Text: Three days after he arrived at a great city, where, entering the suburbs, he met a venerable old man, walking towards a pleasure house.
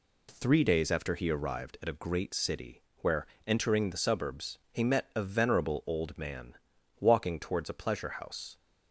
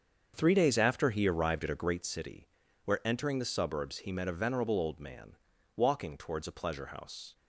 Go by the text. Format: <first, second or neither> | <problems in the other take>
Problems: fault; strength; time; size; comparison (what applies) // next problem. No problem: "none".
first | starts louder than the rest; until 2.0 s; 7 dB